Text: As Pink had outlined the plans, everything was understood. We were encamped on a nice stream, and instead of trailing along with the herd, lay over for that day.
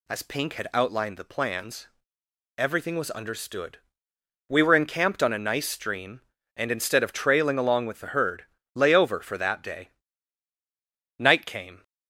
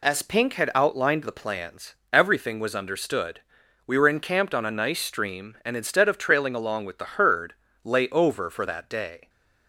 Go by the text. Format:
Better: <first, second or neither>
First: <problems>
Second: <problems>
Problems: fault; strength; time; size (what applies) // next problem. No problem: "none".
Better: second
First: goes on to say "Night came"; noticeable; from 11.1 s on; 0.64 s long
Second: none